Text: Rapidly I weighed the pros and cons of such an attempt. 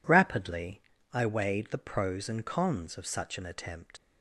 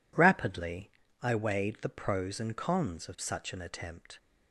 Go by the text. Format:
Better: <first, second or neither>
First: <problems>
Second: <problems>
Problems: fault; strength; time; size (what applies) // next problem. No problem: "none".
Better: second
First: pauses between "Rapidly" and "I"; slight; at 0.8 s; 0.32 s long // leaves "attempt" unfinished; at 3.9 s; 50 ms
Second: pauses between "Rapidly" and "I"; slight; at 0.9 s; 0.32 s long